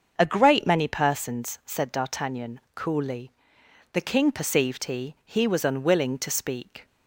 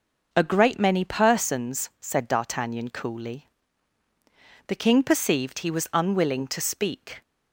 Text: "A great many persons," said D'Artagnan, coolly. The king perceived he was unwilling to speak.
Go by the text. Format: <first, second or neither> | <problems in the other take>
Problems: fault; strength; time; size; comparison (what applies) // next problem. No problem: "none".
second | starts louder than the rest; until 1.1 s; 6.5 dB // says "he" twice; at 5.2 s